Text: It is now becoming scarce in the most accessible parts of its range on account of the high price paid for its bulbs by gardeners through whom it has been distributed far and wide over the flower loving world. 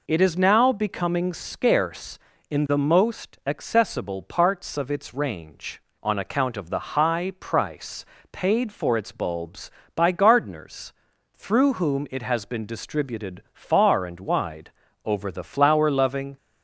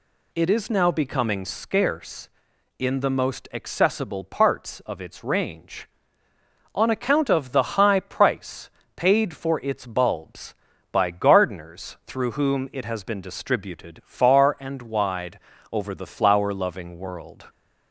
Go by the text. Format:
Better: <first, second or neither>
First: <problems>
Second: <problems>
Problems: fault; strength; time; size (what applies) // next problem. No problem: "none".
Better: second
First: pauses between "price" and "paid"; slight; at 8.0 s; 0.26 s long // pauses between "gardeners" and "through"; at 10.9 s; 0.42 s long // pauses between "wide" and "over"; slight; at 14.7 s; 0.34 s long // stops before "world"; at 16.3 s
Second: pauses between "price" and "paid"; slight; at 8.6 s; 0.26 s long // pauses between "wide" and "over"; slight; at 15.3 s; 0.32 s long